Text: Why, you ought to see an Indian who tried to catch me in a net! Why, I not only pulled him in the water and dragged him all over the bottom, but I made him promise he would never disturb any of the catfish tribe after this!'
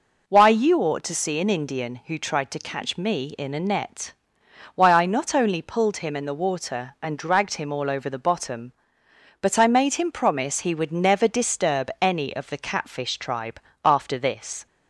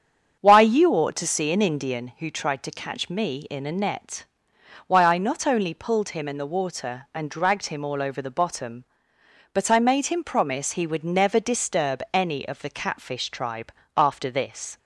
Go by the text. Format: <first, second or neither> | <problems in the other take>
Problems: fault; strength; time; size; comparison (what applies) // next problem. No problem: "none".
first | starts louder than the rest; strong; until 2.1 s; 7.5 dB // pauses between "tribe" and "after"; slight; at 13.7 s; 0.24 s long; slight in the first